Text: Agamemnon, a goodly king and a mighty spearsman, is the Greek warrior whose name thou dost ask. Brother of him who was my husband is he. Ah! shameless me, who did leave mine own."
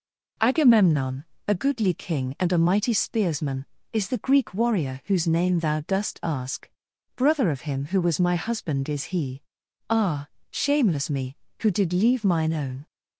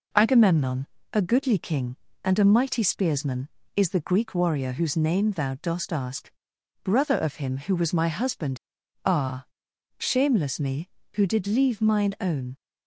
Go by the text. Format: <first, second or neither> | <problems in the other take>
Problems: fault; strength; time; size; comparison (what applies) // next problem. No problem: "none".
first | skips "is he"; at 8.8 s